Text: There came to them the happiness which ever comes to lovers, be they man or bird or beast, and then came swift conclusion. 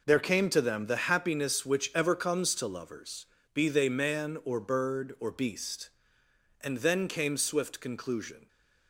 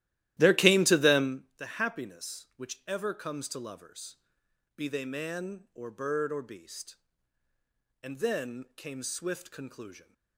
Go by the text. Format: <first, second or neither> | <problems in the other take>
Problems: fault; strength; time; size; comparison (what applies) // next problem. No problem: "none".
first | starts louder than the rest; strong; until 1.4 s; 14.5 dB